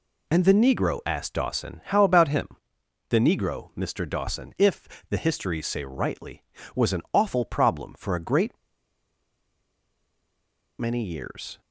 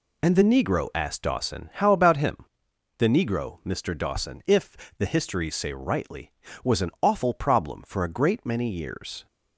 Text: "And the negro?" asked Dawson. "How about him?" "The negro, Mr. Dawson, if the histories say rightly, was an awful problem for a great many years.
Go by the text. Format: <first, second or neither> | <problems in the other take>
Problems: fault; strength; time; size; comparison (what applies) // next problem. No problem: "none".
second | pauses between "if" and "the"; slight; at 4.8 s; 0.22 s long; slight in the second // pauses between "great" and "many"; strong; at 8.5 s; 2.2 s long